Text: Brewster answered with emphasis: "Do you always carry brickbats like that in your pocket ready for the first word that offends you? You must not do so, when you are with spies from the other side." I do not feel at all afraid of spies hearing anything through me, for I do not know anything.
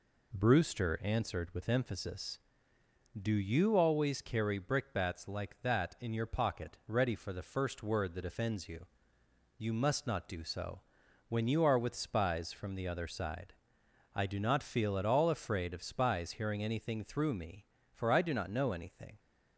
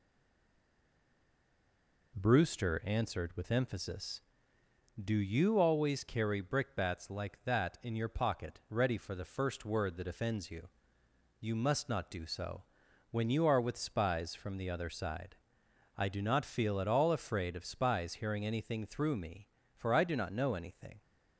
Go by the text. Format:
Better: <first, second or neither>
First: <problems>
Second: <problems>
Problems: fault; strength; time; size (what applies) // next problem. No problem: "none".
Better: first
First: none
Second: stays silent before the first word; until 2.1 s; 2.1 s long